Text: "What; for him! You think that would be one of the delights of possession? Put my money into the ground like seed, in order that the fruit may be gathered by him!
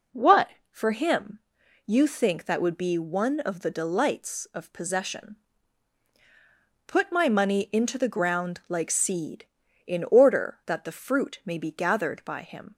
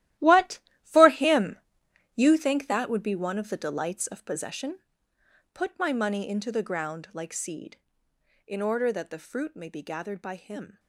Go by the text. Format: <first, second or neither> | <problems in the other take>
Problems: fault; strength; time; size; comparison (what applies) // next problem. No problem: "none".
first | gets quieter; strong; throughout; 13.5 dB